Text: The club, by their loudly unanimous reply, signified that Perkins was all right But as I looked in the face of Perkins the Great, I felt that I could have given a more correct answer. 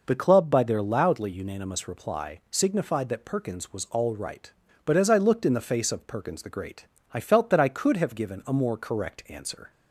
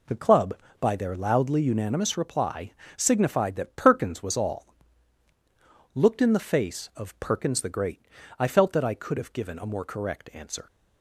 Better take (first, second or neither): first